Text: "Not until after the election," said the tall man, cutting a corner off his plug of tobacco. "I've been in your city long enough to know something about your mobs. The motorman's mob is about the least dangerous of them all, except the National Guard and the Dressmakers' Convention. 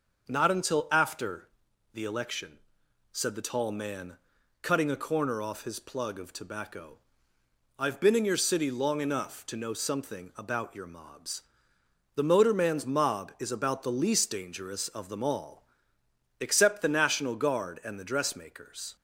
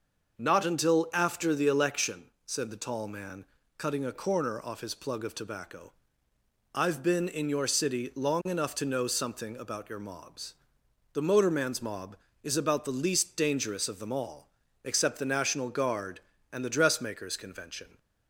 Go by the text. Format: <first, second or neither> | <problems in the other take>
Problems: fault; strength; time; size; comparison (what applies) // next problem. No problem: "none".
second | pauses between "after" and "the"; at 1.4 s; 0.44 s long // stops before "Convention"; at 18.9 s